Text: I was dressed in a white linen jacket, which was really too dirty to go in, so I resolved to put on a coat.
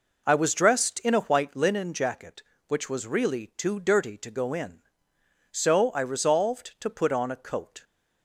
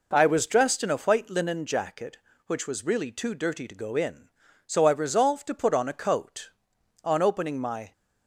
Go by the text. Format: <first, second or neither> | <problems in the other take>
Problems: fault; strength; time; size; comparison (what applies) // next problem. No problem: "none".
first | goes on to say "On opening my"; noticeable; from 7.0 s on; 0.90 s long